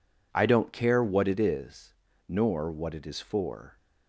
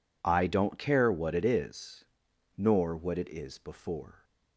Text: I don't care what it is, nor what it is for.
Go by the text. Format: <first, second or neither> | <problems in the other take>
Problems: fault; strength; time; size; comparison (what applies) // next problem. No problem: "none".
first | says "before" for "for"; at 3.5 s